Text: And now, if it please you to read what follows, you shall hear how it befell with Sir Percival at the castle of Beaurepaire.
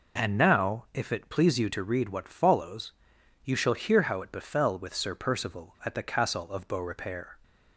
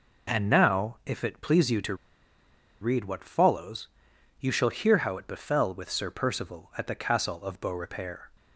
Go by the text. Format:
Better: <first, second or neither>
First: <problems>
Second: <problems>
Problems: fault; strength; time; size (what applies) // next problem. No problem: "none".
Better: first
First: none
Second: pauses between "to" and "read"; noticeable; at 1.9 s; 0.86 s long